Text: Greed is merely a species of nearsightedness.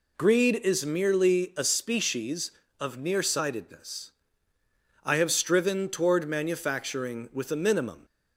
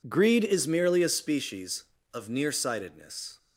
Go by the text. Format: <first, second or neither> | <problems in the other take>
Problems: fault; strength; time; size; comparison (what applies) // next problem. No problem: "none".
second | goes on to say "I have striven toward manufacturing with a minimum"; strong; from 5.0 s on; 3.0 s long